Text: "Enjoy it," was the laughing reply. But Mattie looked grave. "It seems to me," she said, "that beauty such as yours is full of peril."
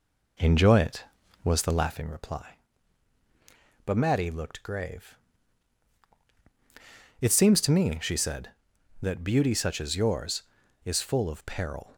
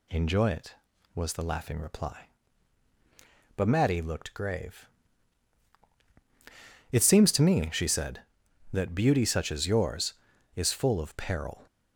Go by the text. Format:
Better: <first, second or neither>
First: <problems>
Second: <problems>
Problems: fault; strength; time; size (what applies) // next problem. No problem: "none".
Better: second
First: starts louder than the rest; until 2.1 s; 3.5 dB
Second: none